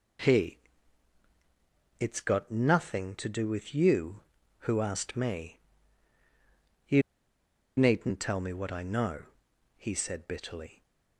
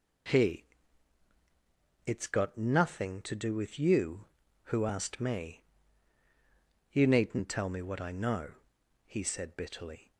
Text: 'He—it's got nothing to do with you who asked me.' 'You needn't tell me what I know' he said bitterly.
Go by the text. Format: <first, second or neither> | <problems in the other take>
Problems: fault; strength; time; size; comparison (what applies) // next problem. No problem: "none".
second | pauses between "You" and "needn't"; noticeable; at 7.0 s; 0.75 s long // pauses between "know" and "he"; noticeable; at 9.2 s; 0.50 s long; noticeable in the second